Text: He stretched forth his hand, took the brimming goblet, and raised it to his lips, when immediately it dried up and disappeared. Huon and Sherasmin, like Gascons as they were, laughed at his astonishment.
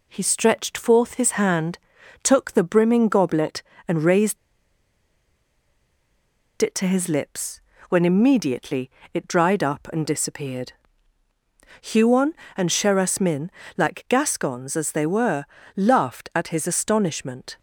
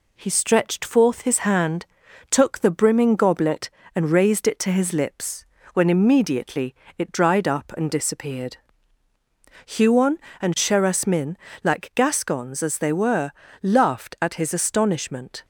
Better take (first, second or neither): second